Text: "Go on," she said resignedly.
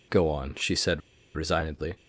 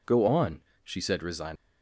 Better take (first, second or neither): second